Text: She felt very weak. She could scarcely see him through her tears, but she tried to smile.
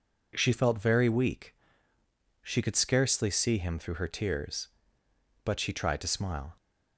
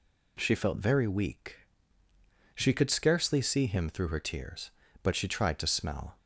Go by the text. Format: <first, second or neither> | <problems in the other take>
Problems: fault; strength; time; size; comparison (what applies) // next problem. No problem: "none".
first | says "smell" for "smile"; at 5.6 s